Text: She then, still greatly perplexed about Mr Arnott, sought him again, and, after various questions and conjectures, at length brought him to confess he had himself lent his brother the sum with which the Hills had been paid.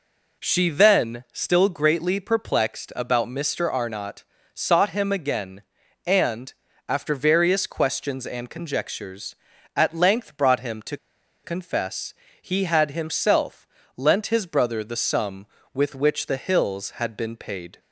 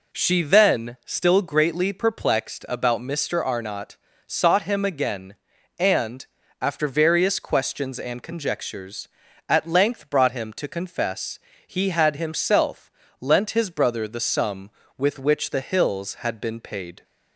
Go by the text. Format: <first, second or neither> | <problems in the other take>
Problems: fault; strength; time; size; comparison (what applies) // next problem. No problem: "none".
second | pauses between "to" and "confess"; noticeable; at 10.9 s; 0.48 s long // pauses between "confess" and "he"; slight; at 12.1 s; 0.26 s long; slight in the second // pauses between "himself" and "lent"; slight; at 13.6 s; 0.30 s long; slight in the second